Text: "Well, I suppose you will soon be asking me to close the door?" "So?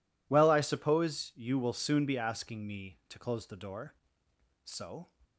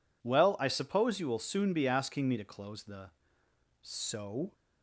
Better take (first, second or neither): first